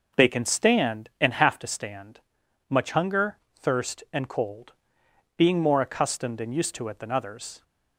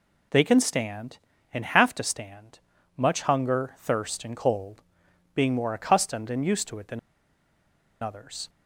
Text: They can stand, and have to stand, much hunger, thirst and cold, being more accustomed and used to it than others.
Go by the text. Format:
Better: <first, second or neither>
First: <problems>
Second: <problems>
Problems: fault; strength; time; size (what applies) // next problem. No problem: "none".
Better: first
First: none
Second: pauses between "than" and "others"; at 6.9 s; 1.0 s long